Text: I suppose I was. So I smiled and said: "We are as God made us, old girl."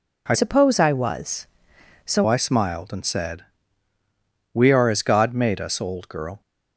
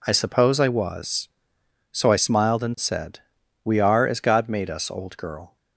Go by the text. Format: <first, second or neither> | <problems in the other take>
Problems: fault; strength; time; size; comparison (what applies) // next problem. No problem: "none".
second | changes voice from "suppose" to "So"; from 0.3 to 2.2 s; 1.9 s long